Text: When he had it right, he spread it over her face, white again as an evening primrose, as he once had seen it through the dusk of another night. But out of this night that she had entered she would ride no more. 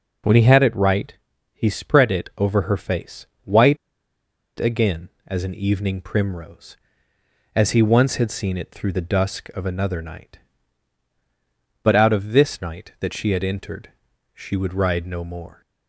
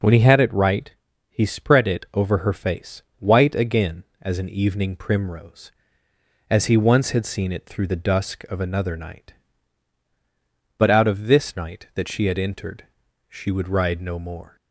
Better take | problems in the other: second | pauses between "white" and "again"; noticeable; at 3.7 s; 0.81 s long // pauses between "entered" and "she"; noticeable; at 13.9 s; 0.46 s long; noticeable in the second

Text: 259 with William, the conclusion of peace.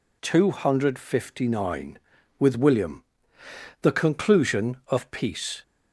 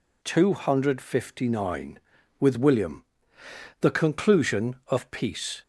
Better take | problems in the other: neither | none

